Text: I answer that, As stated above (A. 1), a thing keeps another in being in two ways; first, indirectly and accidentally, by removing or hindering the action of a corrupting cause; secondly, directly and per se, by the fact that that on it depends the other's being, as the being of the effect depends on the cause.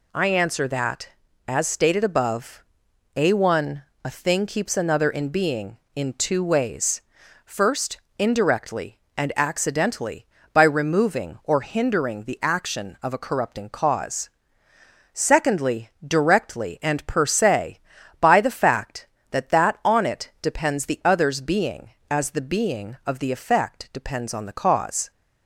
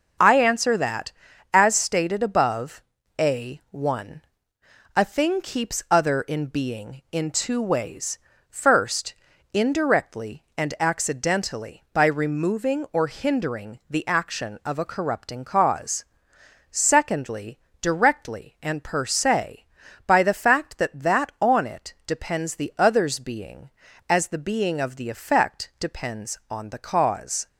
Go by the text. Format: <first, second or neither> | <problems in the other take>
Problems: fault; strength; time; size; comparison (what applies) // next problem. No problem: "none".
first | starts louder than the rest; until 1.6 s; 6.5 dB // says "other" for "another"; at 5.9 s